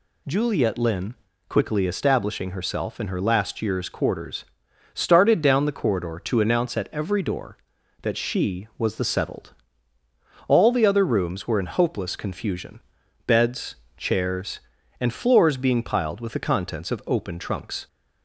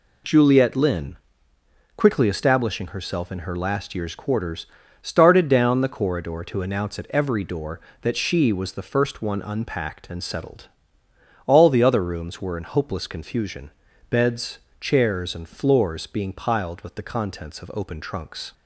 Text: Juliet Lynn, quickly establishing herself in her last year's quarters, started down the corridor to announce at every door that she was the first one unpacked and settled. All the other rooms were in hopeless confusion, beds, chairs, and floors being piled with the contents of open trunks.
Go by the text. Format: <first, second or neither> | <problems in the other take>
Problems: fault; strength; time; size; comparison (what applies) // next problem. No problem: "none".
second | skips "first one unpacked and"; at 9.0 s